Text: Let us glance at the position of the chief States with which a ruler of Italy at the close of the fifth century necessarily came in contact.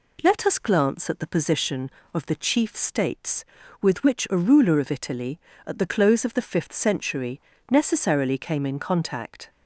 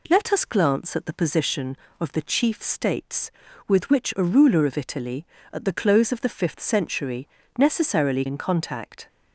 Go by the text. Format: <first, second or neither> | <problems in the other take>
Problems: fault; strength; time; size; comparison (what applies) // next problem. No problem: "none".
first | pauses between "century" and "necessarily"; slight; at 7.2 s; 0.32 s long; slight in the first // skips "came"; at 8.2 s